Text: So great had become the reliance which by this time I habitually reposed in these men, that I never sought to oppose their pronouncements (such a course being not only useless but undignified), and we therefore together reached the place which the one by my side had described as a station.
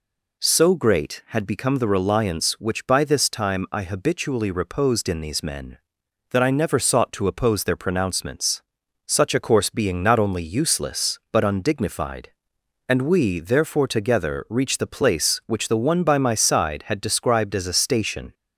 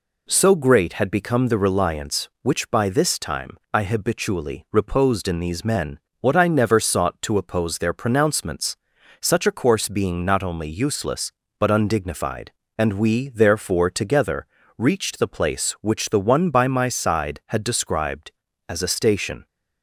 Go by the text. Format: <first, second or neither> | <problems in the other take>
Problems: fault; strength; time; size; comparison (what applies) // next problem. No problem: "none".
first | pauses between "time" and "I"; slight; at 3.5 s; 0.16 s long // says "what" for "that"; at 6.1 s // pauses between "together" and "reached"; slight; at 14.4 s; 0.30 s long